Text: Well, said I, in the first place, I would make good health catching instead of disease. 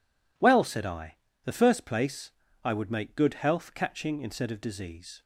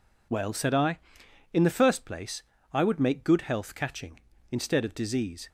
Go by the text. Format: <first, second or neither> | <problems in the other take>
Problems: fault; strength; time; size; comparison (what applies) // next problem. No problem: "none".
second | skips "in"; at 1.3 s